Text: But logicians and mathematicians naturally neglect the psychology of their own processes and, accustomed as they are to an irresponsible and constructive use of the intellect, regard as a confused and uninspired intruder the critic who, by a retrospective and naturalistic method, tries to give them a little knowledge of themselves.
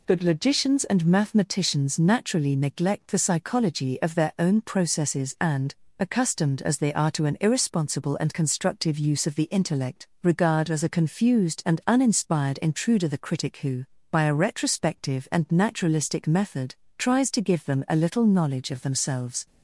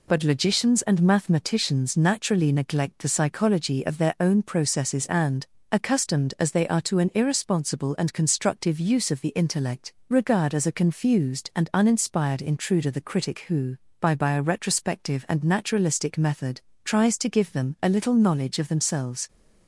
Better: first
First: none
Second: says "by" twice; at 14.1 s

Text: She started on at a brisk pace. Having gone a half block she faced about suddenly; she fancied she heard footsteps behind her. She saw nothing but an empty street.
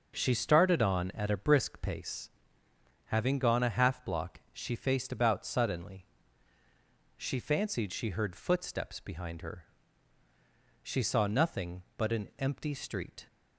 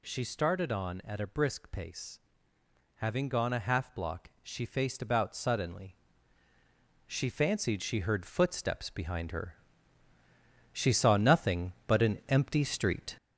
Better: first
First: none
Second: gets louder; noticeable; throughout; 4.5 dB

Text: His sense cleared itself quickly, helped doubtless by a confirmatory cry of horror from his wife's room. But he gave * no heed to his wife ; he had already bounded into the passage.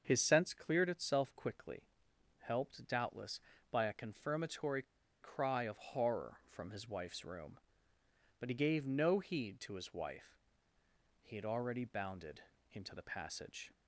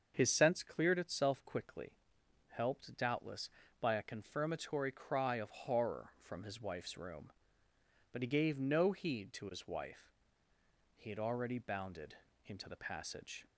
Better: second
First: starts louder than the rest; until 1.0 s; 6.5 dB // pauses between "confirmatory" and "cry"; at 4.8 s; 0.38 s long // pauses between "bounded" and "into"; slight; at 12.4 s; 0.30 s long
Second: starts louder than the rest; until 1.1 s; 6.5 dB // pauses between "bounded" and "into"; slight; at 12.1 s; 0.30 s long

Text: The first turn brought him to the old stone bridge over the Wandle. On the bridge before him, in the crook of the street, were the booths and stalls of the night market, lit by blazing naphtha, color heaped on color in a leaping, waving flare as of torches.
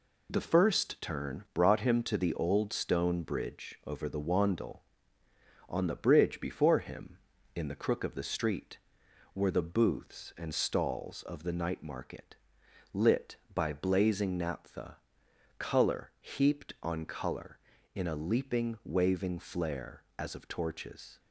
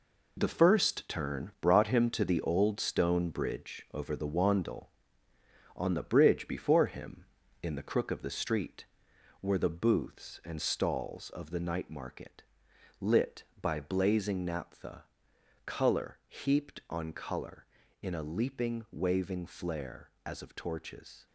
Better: first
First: none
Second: gets quieter; strong; throughout; 9 dB

